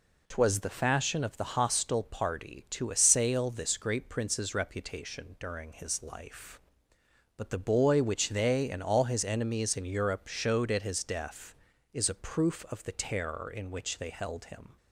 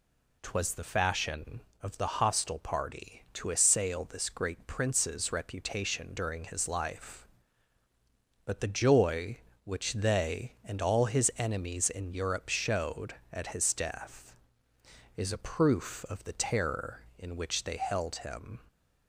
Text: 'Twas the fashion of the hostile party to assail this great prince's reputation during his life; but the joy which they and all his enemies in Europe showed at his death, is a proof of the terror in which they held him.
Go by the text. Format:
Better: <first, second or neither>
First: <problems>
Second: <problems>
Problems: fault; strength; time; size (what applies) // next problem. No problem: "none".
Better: second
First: says "boy" for "joy"; at 7.5 s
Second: none